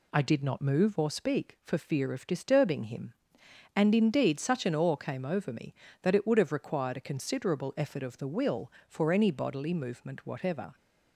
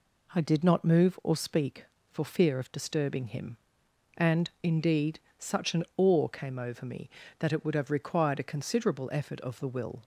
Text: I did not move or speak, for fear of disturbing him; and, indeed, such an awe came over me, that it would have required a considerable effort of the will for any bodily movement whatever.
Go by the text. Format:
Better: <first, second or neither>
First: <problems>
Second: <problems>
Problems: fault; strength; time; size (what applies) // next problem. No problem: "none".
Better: first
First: none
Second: stops before "for any bodily movement whatever"; at 10.0 s